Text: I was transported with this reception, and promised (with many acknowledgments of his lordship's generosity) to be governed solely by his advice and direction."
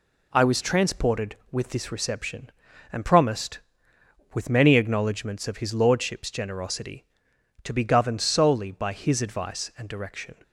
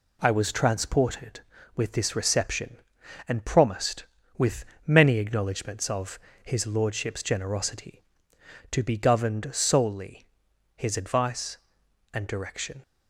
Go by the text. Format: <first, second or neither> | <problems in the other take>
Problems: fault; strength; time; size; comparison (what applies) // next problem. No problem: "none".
first | pauses between "with" and "many"; slight; at 4.6 s; 0.20 s long // pauses between "of" and "his"; slight; at 6.1 s; 0.26 s long // skips "by"; at 10.5 s